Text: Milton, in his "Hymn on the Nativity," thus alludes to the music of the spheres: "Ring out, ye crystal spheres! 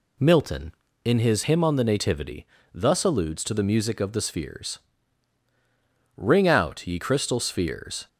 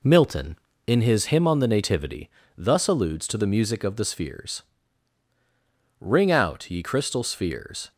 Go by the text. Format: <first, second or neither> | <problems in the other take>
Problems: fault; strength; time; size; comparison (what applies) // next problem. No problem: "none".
first | gets quieter; noticeable; throughout; 4 dB